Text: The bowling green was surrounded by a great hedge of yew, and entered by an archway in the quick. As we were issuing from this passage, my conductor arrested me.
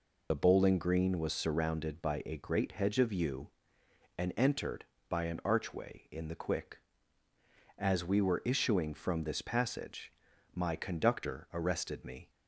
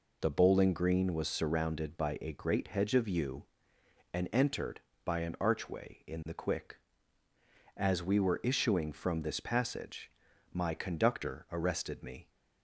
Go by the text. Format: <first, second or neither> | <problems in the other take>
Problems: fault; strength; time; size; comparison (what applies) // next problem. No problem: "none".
second | loses the start of "The"; at 0.3 s; 35 ms